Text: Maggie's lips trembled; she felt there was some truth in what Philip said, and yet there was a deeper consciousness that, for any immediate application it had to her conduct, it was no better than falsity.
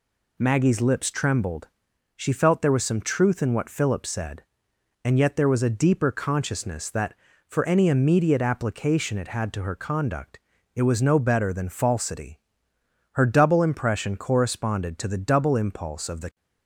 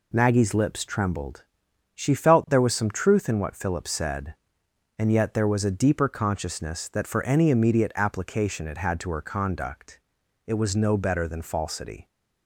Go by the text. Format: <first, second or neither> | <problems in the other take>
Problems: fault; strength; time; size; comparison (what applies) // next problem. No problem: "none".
second | goes on to say "Her double impression corresponded to the double impulse of the"; strong; from 13.1 s on; 3.2 s long